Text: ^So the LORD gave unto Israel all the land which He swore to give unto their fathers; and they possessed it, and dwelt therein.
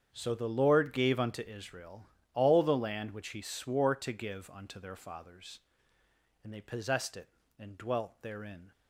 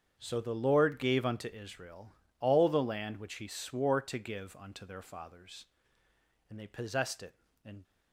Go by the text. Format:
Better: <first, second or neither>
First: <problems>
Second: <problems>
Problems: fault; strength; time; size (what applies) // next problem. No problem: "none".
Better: first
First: starts louder than the rest; strong; until 1.1 s; 8 dB // pauses between "Israel" and "all"; slight; at 2.0 s; 0.26 s long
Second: starts louder than the rest; strong; until 1.2 s; 7.5 dB // pauses between "Israel" and "all"; slight; at 2.1 s; 0.26 s long // stops before "dwelt therein"; at 7.8 s